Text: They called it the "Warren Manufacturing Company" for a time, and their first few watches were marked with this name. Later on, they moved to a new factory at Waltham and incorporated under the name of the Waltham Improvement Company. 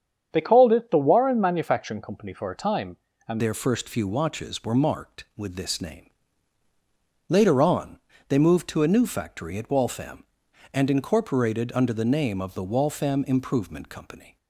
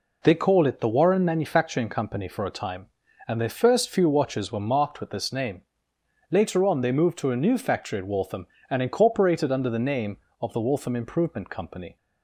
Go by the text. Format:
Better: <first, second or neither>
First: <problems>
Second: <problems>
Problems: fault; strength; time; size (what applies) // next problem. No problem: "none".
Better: second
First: starts louder than the rest; strong; until 1.3 s; 8 dB // changes voice at "their"; from 3.3 s on; 11.0 s long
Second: none